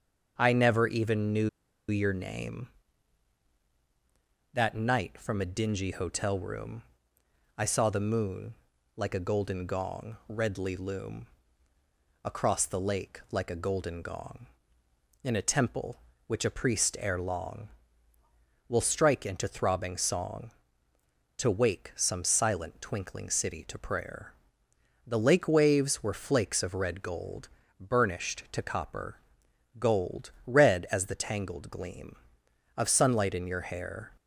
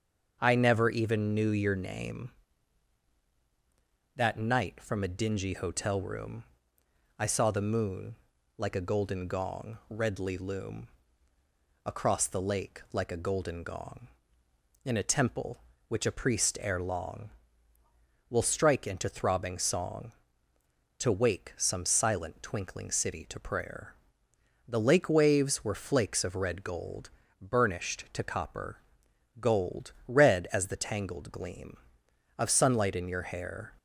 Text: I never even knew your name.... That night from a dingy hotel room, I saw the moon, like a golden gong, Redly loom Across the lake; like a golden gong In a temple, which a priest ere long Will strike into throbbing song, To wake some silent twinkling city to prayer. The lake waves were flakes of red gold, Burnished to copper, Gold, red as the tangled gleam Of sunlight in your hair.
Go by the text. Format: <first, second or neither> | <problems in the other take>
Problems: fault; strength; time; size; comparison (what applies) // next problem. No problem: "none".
second | starts louder than the rest; until 1.4 s; 6.5 dB; also in the second // pauses between "knew" and "your"; at 1.4 s; 0.40 s long // pauses between "loom" and "Across"; noticeable; at 11.2 s; 0.96 s long; noticeable in the second